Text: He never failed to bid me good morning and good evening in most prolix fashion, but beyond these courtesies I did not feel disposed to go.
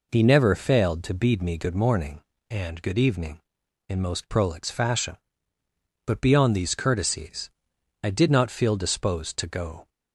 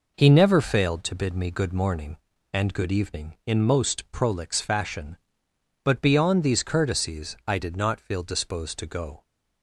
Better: second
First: says "bead" for "bid"; at 1.1 s // pauses between "courtesies" and "I"; noticeable; at 7.4 s; 0.54 s long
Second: none

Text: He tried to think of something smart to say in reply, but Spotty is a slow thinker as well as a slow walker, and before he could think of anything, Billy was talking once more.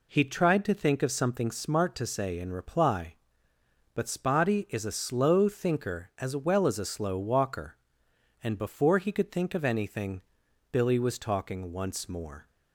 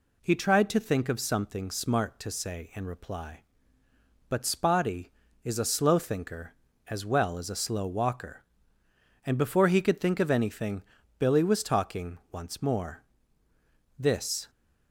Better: first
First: none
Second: goes on to say "This"; from 13.9 s on; 0.52 s long

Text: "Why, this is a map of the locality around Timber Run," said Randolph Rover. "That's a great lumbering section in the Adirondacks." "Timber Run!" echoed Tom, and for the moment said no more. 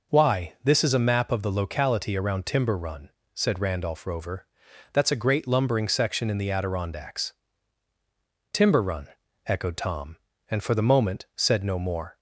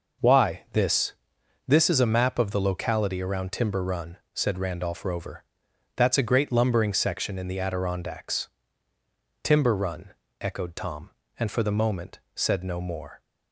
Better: first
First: none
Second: says "this" twice; at 1.6 s // pauses between "moment" and "said"; slight; at 12.1 s; 0.16 s long

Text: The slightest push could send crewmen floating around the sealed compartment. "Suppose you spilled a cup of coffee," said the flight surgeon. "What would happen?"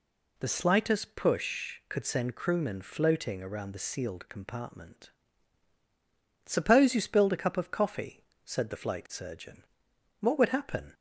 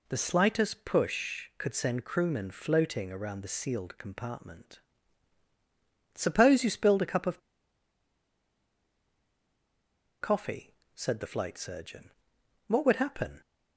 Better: first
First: none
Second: pauses between "of" and "coffee"; strong; at 7.3 s; 2.8 s long

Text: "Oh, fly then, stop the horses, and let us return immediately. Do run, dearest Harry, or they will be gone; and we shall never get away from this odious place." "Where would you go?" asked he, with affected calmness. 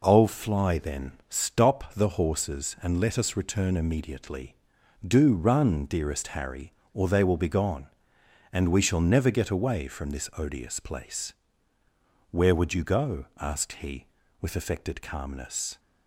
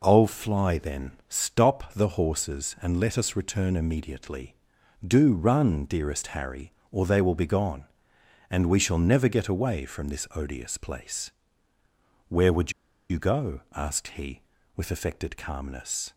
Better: first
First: none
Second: pauses between "would" and "you"; at 12.7 s; 0.37 s long

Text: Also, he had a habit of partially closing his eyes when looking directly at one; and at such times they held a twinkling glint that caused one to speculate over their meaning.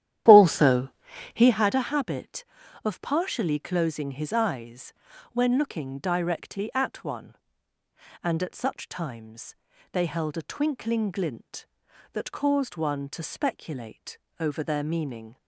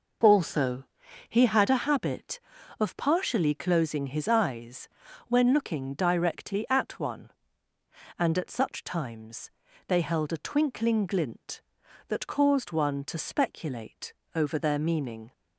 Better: second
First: starts louder than the rest; strong; until 1.6 s; 11.5 dB // pauses between "eyes" and "when"; at 4.9 s; 0.38 s long // pauses between "times" and "they"; at 9.5 s; 0.38 s long // pauses between "speculate" and "over"; slight; at 14.1 s; 0.18 s long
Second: pauses between "eyes" and "when"; at 4.8 s; 0.38 s long // pauses between "times" and "they"; at 9.4 s; 0.38 s long // pauses between "speculate" and "over"; slight; at 14.1 s; 0.18 s long

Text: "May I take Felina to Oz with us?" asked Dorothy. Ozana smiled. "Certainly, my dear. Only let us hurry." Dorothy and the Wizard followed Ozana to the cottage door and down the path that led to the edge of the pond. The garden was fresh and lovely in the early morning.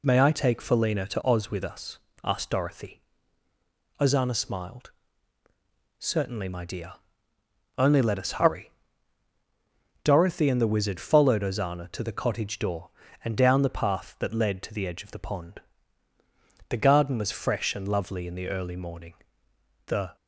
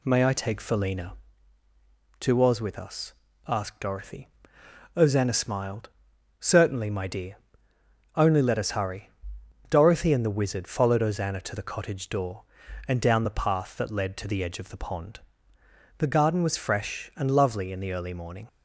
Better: second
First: goes on to say "The"; slight; from 19.8 s on; 0.28 s long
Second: none

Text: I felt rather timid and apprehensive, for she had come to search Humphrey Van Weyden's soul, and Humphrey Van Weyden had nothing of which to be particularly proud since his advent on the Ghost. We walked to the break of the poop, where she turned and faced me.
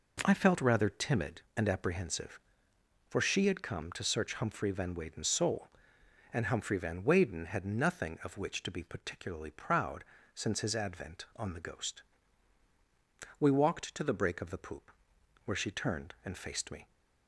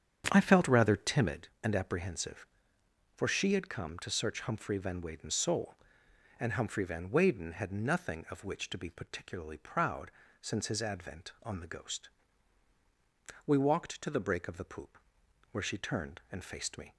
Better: first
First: pauses between "proud" and "since"; slight; at 10.0 s; 0.32 s long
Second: starts louder than the rest; strong; until 1.5 s; 8 dB // pauses between "proud" and "since"; slight; at 10.0 s; 0.32 s long

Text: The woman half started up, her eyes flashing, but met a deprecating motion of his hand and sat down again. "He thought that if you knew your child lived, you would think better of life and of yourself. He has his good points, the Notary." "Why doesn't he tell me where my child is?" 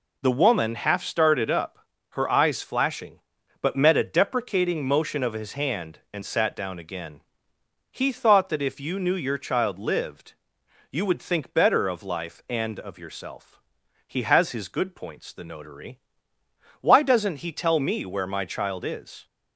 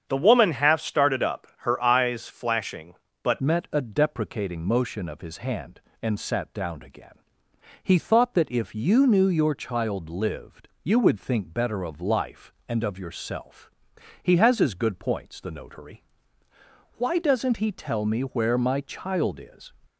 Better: first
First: none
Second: starts louder than the rest; strong; until 1.0 s; 7.5 dB // changes voice at "met"; from 3.4 s on; 16.3 s long

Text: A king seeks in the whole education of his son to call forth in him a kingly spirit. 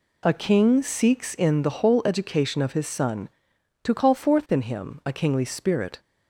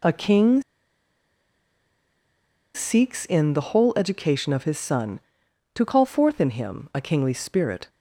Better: first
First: none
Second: pauses between "king" and "seeks"; strong; at 0.6 s; 2.1 s long

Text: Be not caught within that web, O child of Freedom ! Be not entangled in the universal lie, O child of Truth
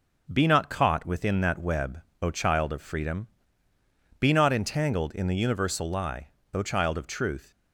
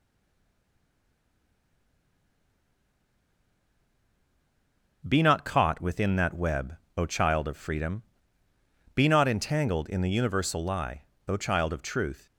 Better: first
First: none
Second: stays silent before the first word; strong; until 5.0 s; 5.0 s long

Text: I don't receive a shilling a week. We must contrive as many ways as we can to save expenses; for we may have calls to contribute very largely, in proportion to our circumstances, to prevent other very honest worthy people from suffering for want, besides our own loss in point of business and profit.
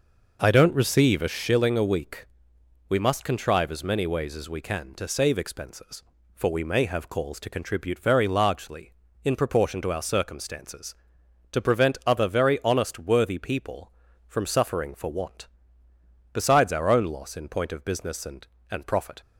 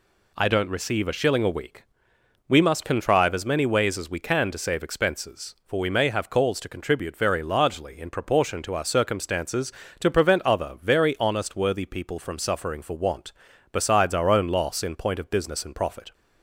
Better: second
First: says "and" twice; at 18.7 s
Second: none

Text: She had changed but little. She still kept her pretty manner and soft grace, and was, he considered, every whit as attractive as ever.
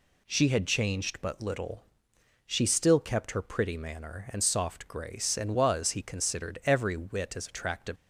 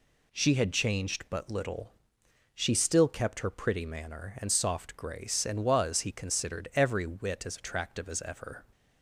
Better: second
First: stops before "as ever"; at 7.9 s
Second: none

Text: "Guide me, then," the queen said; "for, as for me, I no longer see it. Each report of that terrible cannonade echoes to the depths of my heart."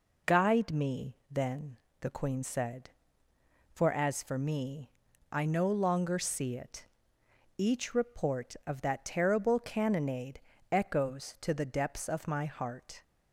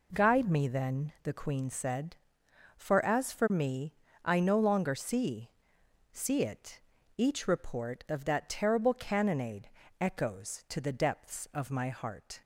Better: first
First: pauses between "cannonade" and "echoes"; slight; at 10.3 s; 0.32 s long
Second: says "see" twice; at 6.1 s // pauses between "cannonade" and "echoes"; slight; at 9.6 s; 0.30 s long

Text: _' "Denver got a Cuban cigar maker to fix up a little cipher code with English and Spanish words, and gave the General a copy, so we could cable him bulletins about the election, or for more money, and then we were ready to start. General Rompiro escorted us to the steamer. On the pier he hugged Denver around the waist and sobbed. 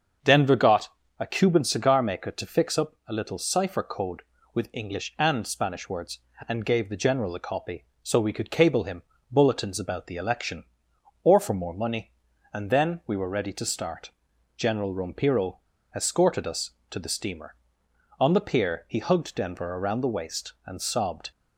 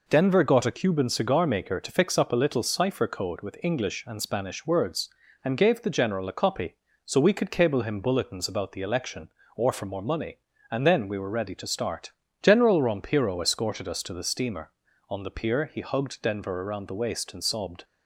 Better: second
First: starts louder than the rest; until 1.4 s; 6.5 dB // pauses between "got" and "a"; slight; at 0.9 s; 0.28 s long // pauses between "him" and "bulletins"; slight; at 9.0 s; 0.28 s long // pauses between "Rompiro" and "escorted"; slight; at 15.6 s; 0.32 s long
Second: none

